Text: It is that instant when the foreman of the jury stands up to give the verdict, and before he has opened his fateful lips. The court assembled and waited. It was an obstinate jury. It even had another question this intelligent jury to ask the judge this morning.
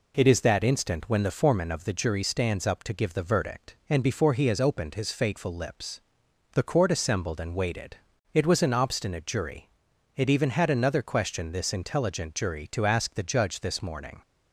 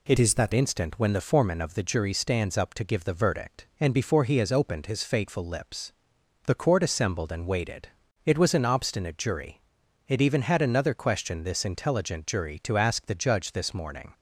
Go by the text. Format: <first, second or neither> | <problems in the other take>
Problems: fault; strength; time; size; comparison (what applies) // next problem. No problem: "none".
first | changes voice from "is" to "that"; from 0.1 to 0.5 s; 0.4 s long